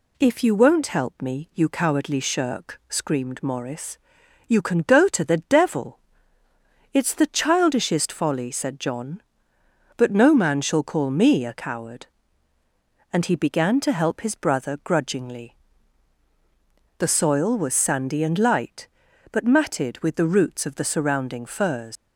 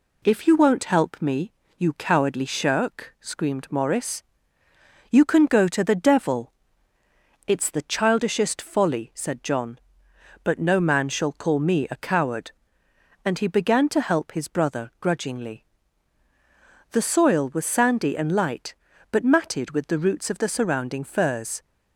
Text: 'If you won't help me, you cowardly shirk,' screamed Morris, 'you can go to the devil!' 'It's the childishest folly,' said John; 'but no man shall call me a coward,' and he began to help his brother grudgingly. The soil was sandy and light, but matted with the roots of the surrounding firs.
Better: second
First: leaves "firs" unfinished; at 21.9 s; 115 ms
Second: none

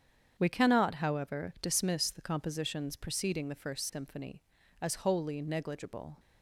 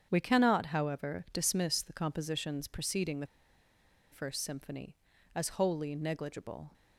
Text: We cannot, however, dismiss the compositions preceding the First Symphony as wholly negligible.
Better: first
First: starts louder than the rest; strong; until 1.3 s; 8 dB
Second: starts louder than the rest; strong; until 1.1 s; 8 dB // pauses between "the" and "First"; noticeable; at 3.2 s; 0.85 s long

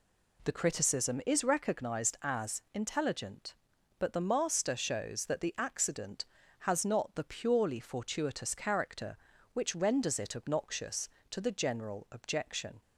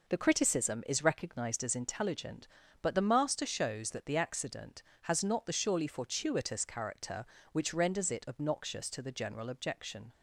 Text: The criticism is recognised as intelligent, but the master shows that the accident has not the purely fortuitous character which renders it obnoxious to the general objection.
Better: first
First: none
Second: says "surely" for "purely"; at 5.5 s

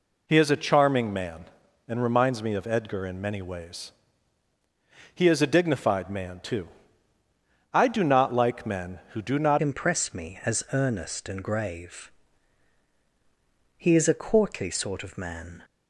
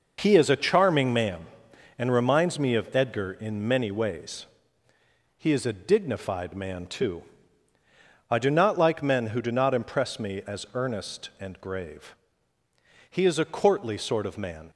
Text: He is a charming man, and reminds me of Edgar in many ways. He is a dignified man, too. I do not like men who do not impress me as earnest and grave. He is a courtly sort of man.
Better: second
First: changes voice at "impress"; from 9.6 s on; 6.0 s long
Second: none

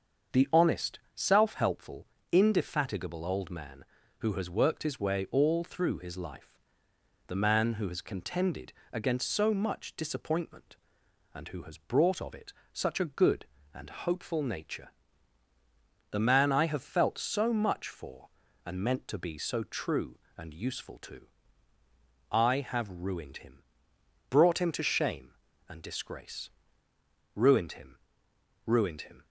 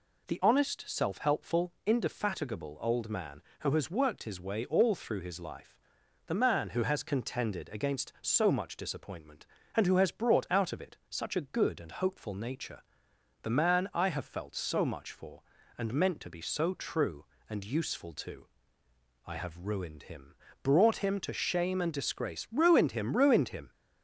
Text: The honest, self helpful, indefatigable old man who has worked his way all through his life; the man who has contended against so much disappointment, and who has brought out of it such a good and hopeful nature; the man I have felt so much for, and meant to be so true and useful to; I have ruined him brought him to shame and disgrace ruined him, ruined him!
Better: second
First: starts louder than the rest; until 1.5 s; 6.5 dB // pauses between "contended" and "against"; slight; at 8.7 s; 0.22 s long // skips "out"; at 12.2 s // pauses between "it" and "such"; slight; at 12.5 s; 0.18 s long // pauses between "him" and "brought"; noticeable; at 23.6 s; 0.66 s long // pauses between "disgrace" and "ruined"; noticeable; at 26.5 s; 0.84 s long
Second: pauses between "him" and "brought"; slight; at 20.3 s; 0.26 s long

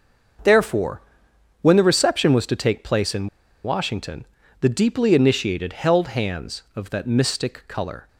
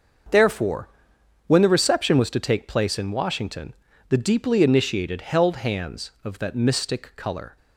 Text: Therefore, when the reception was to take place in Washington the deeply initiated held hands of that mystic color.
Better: second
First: starts louder than the rest; until 2.0 s; 6 dB // pauses between "in" and "Washington"; at 3.2 s; 0.36 s long // pauses between "Washington" and "the"; slight; at 4.2 s; 0.36 s long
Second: starts louder than the rest; until 1.8 s; 6 dB // pauses between "Washington" and "the"; slight; at 3.7 s; 0.36 s long

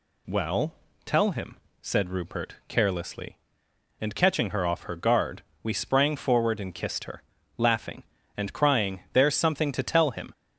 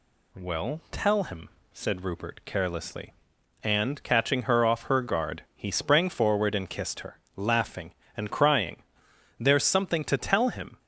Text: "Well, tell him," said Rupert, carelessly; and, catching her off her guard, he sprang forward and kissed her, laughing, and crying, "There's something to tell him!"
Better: second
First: says "we" for "he"; at 5.6 s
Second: none

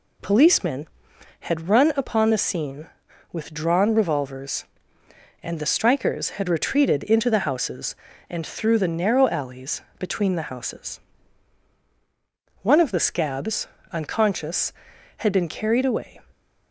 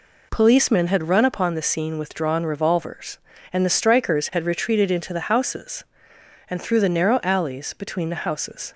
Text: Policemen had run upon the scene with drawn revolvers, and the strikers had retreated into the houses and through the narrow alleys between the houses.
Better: second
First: pauses between "alleys" and "between"; slight; at 9.8 s; 0.18 s long // goes on to say "One of the scabs unconscious had been carried away"; strong; from 12.6 s on; 3.5 s long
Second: none

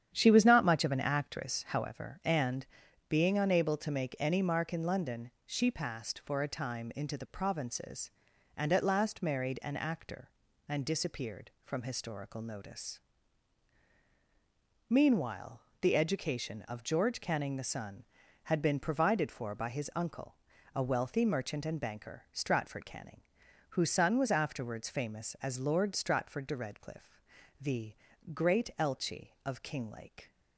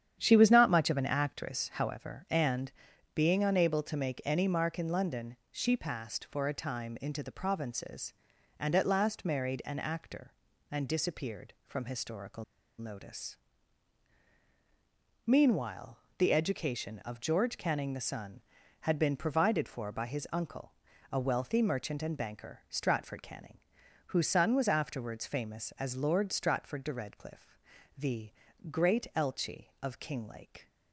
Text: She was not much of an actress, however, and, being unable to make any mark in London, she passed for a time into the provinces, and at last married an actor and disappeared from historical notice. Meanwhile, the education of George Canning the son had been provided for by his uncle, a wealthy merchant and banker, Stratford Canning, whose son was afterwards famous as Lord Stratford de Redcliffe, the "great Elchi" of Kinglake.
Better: first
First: starts louder than the rest; strong; until 1.1 s; 9.5 dB // pauses between "the" and "great"; at 27.9 s; 0.40 s long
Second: starts louder than the rest; strong; until 1.2 s; 9.5 dB // pauses between "historical" and "notice"; slight; at 12.4 s; 0.35 s long // pauses between "the" and "great"; at 28.3 s; 0.40 s long

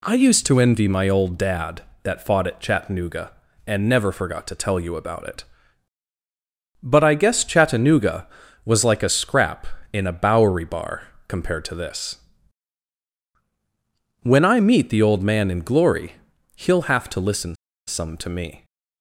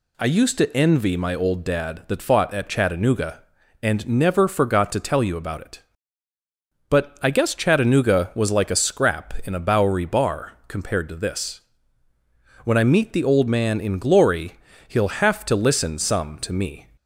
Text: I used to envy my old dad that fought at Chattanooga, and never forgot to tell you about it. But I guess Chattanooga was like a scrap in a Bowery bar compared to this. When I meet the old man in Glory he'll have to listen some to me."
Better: second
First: pauses between "bar" and "compared"; slight; at 11.0 s; 0.22 s long // pauses between "Glory" and "he'll"; at 16.1 s; 0.42 s long // pauses between "listen" and "some"; slight; at 17.5 s; 0.31 s long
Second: pauses between "Glory" and "he'll"; slight; at 14.5 s; 0.36 s long

